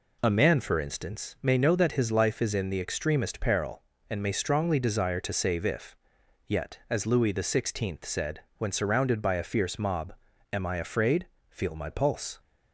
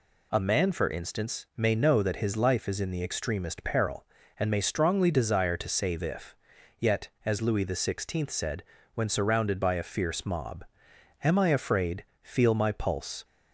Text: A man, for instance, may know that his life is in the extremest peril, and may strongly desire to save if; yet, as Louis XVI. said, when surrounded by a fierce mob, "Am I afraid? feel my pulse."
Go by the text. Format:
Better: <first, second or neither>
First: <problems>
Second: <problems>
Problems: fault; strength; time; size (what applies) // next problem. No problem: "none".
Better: neither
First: none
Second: none